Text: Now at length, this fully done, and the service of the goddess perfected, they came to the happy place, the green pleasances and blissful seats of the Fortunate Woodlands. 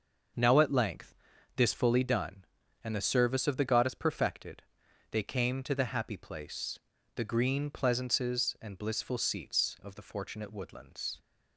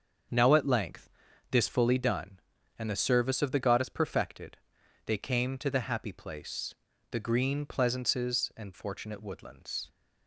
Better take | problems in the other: first | starts louder than the rest; until 1.7 s; 6.5 dB; noticeable in the first // skips "blissful seats of the"; at 8.7 s

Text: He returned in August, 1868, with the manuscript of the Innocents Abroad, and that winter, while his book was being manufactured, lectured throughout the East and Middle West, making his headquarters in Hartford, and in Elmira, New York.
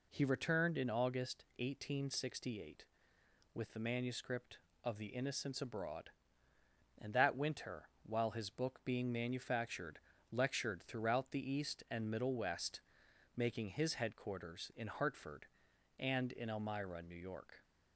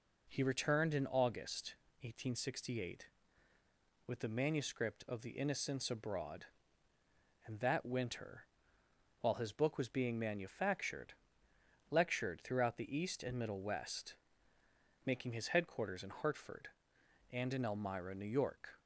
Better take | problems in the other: second | skips "was"; at 8.8 s

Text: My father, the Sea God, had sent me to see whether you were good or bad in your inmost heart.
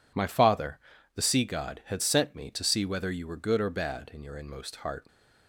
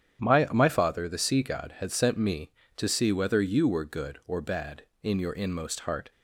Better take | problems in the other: first | starts louder than the rest; strong; until 1.2 s; 9.5 dB // says "My" twice; at 0.5 s

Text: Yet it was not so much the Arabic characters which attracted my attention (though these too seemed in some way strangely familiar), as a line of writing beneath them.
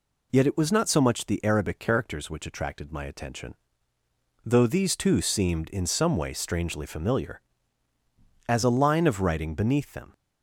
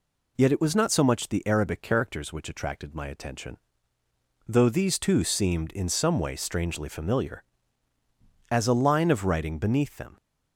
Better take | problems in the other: neither | none

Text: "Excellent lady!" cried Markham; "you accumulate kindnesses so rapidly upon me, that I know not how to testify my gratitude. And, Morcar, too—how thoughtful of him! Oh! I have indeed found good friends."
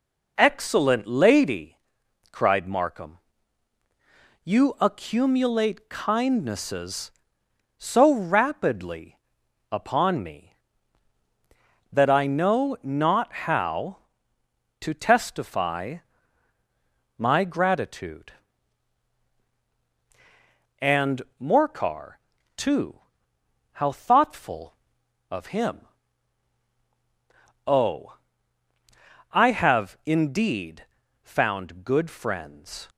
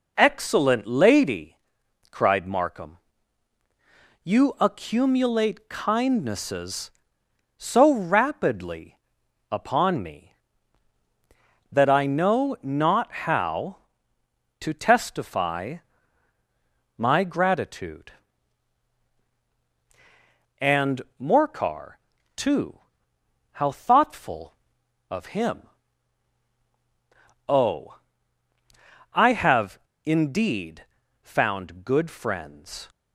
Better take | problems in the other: first | pauses between "rapidly" and "upon"; noticeable; at 8.9 s; 0.54 s long; noticeable in the first // pauses between "testify" and "my"; at 15.7 s; 1.2 s long; also in the first // pauses between "have" and "indeed"; slight; at 29.7 s; 0.27 s long // pauses between "indeed" and "found"; at 30.8 s; 0.38 s long; also in the first

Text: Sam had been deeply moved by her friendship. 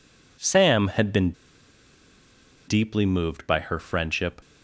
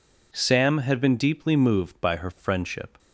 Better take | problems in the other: second | pauses between "been" and "deeply"; strong; at 1.3 s; 1.3 s long

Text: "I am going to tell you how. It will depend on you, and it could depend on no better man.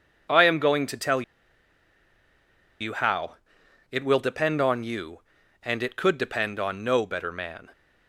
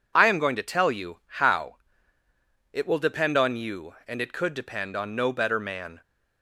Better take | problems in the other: second | pauses between "tell" and "you"; strong; at 1.2 s; 1.5 s long

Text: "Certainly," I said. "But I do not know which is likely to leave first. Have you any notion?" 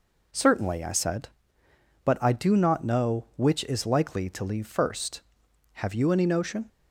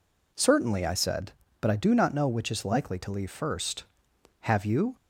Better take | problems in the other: first | stops before "any notion"; at 4.9 s

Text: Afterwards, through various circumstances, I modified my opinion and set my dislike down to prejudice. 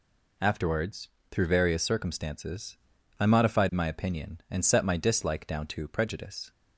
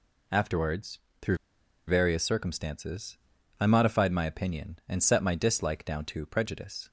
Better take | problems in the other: first | pauses between "through" and "various"; noticeable; at 1.3 s; 0.50 s long

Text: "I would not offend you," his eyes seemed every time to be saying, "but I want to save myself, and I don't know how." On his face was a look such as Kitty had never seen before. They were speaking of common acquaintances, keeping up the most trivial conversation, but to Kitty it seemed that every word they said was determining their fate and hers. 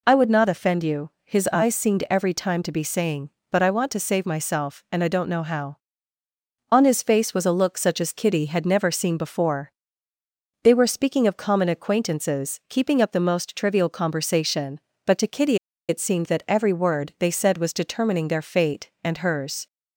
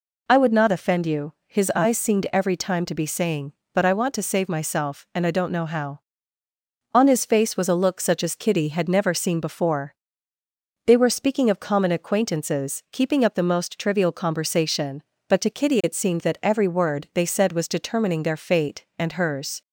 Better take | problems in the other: second | pauses between "Kitty" and "it"; slight; at 15.5 s; 0.31 s long

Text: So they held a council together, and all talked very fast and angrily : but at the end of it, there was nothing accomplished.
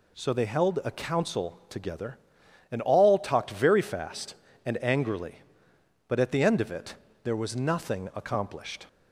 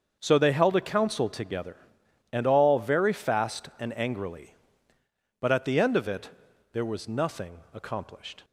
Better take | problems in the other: first | starts louder than the rest; until 1.2 s; 6.5 dB // skips "talked"; at 2.7 s

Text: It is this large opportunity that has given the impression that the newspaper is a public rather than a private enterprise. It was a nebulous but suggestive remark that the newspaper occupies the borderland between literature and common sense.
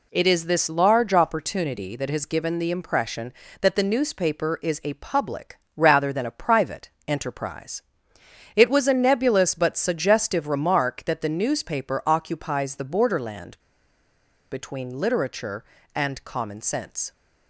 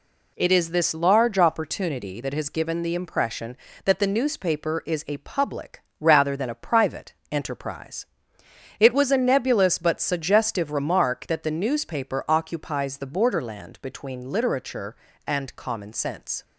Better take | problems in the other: second | pauses between "public" and "rather"; slight; at 5.5 s; 0.20 s long; slight in the second // pauses between "private" and "enterprise"; slight; at 6.9 s; 0.16 s long; slight in the second // pauses between "borderland" and "between"; noticeable; at 13.5 s; 0.95 s long

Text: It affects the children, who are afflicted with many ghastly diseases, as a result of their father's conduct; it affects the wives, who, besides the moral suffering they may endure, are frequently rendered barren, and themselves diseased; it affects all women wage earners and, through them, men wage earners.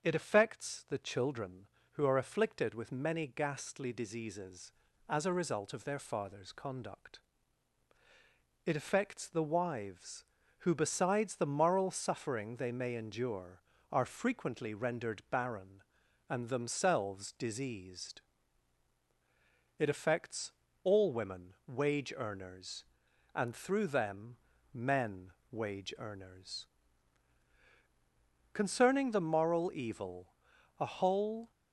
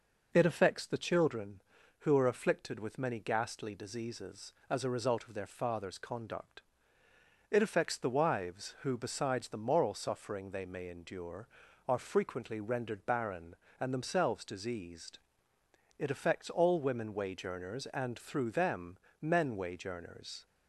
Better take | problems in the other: second | starts louder than the rest; until 1.0 s; 6.5 dB // pauses between "affects" and "all"; slight; at 20.5 s; 0.32 s long // pauses between "men" and "wage"; slight; at 25.3 s; 0.18 s long // goes on to say "Concerning the moral evil a whole"; strong; from 28.5 s on; 2.9 s long

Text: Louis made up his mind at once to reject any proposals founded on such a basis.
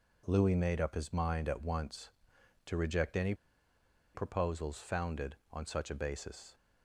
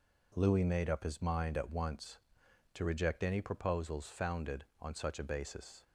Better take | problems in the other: second | pauses between "any" and "proposals"; noticeable; at 3.3 s; 0.80 s long

